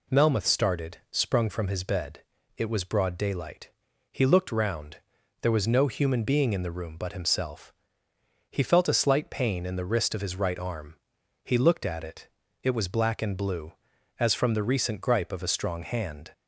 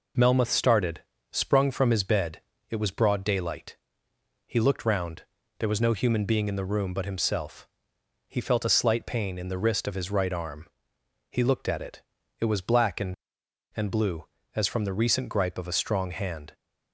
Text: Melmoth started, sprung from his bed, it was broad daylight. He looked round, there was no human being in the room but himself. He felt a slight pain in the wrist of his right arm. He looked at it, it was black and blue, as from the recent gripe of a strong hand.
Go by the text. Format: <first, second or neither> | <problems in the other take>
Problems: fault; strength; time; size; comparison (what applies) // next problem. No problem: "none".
first | says "and" twice; at 13.7 s